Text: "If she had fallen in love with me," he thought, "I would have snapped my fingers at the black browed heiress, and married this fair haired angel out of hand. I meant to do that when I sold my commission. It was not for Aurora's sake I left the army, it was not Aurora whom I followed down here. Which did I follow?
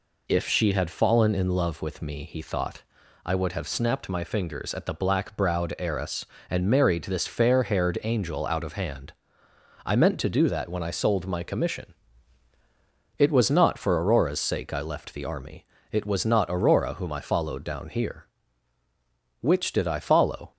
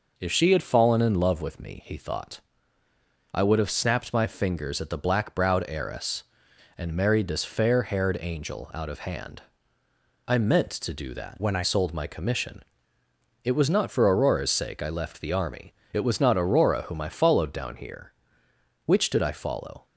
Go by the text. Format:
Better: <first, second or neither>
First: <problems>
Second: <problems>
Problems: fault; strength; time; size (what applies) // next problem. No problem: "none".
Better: first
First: none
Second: changes voice from "when" to "I"; from 11.4 to 11.6 s; 0.2 s long